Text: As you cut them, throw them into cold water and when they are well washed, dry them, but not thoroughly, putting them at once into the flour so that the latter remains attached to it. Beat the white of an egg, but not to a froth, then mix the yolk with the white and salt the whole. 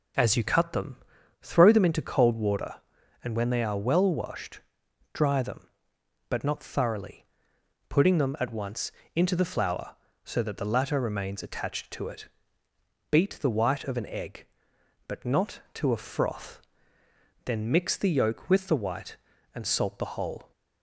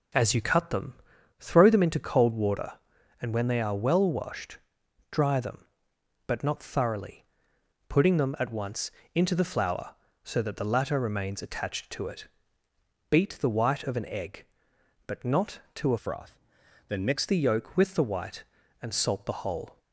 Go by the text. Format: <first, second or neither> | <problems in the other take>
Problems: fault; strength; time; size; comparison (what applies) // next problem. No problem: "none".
first | pauses between "once" and "into"; slight; at 8.9 s; 0.24 s long; slight in the first // changes voice from "froth" to "mix"; from 15.9 to 17.2 s; 1.3 s long